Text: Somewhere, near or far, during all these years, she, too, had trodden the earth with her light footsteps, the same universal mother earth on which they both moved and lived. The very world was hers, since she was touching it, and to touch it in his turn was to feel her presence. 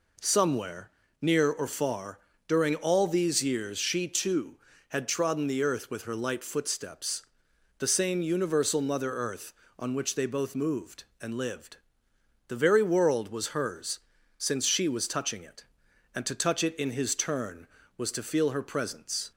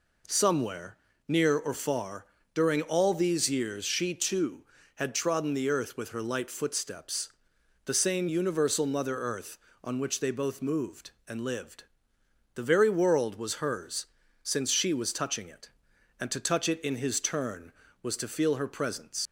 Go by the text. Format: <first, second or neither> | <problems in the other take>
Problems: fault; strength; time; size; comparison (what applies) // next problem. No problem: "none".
first | leaves "presence" unfinished; at 19.2 s; 105 ms